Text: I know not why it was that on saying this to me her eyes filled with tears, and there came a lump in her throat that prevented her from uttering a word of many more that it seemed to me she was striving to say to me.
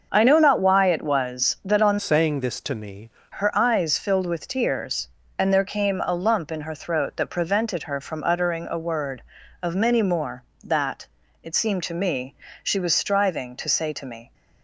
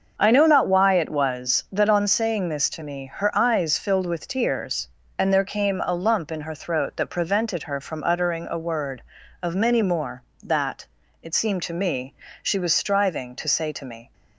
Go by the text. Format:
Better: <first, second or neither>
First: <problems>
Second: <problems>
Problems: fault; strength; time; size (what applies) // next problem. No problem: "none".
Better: second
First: starts louder than the rest; until 1.1 s; 6 dB // changes voice from "saying" to "me"; from 1.9 to 3.0 s; 1.1 s long // pauses between "that" and "it"; slight; at 11.0 s; 0.34 s long // pauses between "me" and "she"; slight; at 12.3 s; 0.30 s long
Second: starts louder than the rest; until 1.1 s; 6.5 dB // pauses between "that" and "it"; slight; at 10.8 s; 0.34 s long // pauses between "me" and "she"; slight; at 12.1 s; 0.30 s long